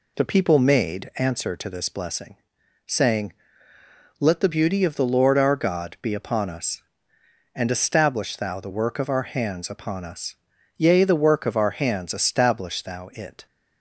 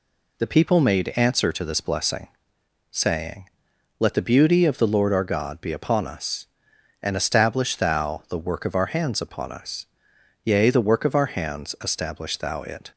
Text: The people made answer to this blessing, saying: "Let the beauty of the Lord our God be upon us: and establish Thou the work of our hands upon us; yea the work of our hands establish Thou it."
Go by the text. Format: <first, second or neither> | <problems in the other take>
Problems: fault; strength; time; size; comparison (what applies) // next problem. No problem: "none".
neither | none